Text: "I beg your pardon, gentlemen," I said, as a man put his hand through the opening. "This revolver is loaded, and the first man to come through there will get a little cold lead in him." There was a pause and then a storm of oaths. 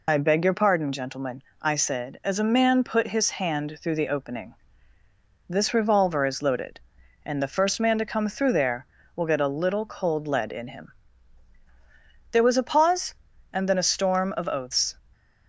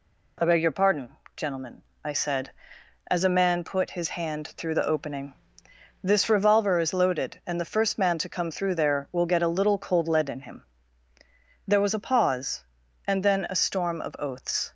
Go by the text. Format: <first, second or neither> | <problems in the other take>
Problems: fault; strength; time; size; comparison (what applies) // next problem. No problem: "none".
second | loses the start of "I"; at 0.0 s; 65 ms